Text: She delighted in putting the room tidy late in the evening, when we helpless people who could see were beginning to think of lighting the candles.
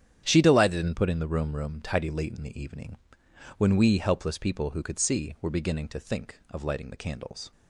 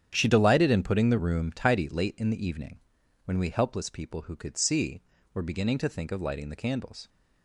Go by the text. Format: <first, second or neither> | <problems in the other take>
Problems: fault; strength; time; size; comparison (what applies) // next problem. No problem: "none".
second | starts louder than the rest; strong; until 1.2 s; 9.5 dB; strong in the second // says "room" twice; at 1.5 s